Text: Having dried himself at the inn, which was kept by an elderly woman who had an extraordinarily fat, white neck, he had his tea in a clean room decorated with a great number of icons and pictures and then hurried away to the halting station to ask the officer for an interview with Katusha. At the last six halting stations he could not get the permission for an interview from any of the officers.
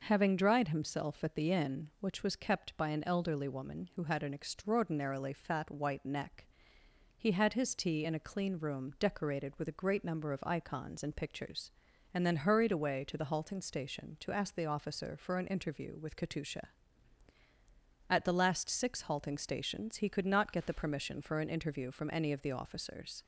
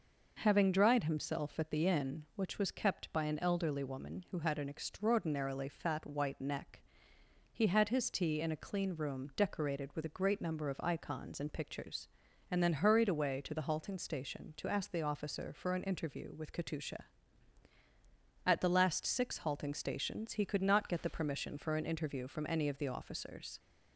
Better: neither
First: none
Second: none

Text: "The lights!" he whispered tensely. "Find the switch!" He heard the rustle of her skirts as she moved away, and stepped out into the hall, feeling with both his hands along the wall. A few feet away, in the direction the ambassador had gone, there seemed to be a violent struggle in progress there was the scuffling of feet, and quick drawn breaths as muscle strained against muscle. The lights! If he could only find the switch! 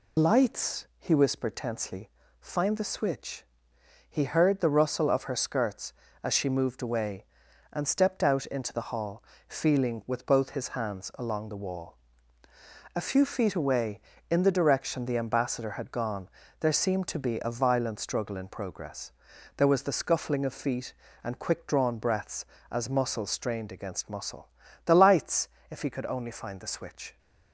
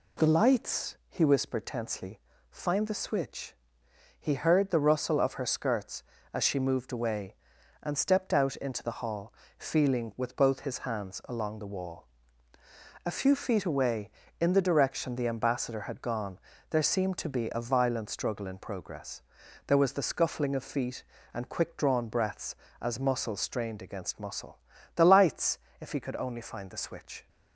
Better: second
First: loses the start of "The"; at 0.1 s; 100 ms // pauses between "progress" and "there"; noticeable; at 19.1 s; 0.46 s long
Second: pauses between "progress" and "there"; noticeable; at 19.2 s; 0.46 s long

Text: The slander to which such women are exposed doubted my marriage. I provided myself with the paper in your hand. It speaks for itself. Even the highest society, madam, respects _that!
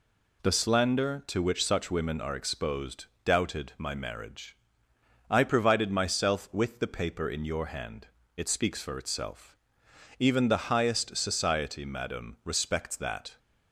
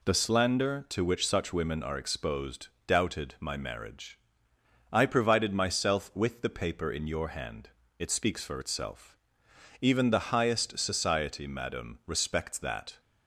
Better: neither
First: pauses between "exposed" and "doubted"; slight; at 3.0 s; 0.20 s long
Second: pauses between "exposed" and "doubted"; slight; at 2.6 s; 0.20 s long

